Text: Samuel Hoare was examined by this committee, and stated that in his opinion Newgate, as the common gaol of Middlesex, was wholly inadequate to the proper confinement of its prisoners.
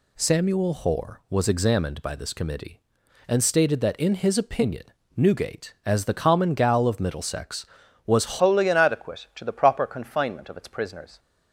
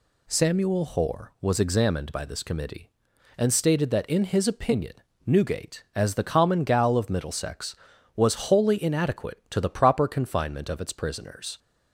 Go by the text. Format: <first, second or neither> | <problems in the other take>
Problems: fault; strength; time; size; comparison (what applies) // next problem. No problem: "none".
second | pauses between "opinion" and "Newgate"; slight; at 4.8 s; 0.32 s long; slight in the second // changes voice at "wholly"; from 8.3 s on; 2.8 s long